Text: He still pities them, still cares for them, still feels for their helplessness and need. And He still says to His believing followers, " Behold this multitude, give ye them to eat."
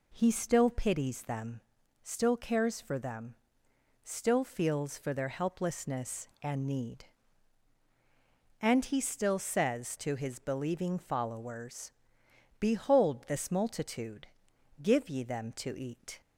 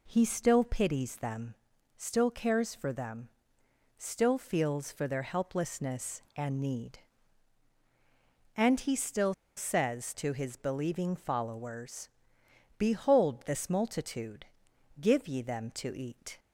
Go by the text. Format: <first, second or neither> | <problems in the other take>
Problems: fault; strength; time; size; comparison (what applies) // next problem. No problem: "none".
first | pauses between "still" and "says"; slight; at 9.3 s; 0.22 s long